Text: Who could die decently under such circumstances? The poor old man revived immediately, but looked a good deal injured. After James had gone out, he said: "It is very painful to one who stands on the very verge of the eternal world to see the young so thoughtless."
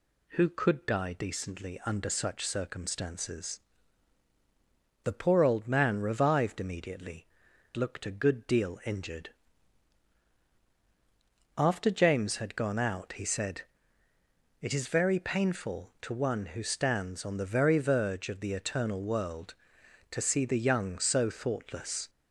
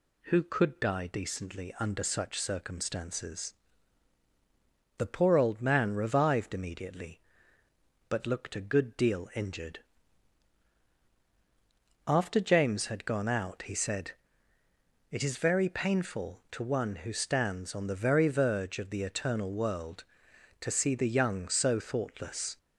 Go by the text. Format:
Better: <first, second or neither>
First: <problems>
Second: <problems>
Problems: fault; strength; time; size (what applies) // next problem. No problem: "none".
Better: second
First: skips "but"; at 7.5 s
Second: none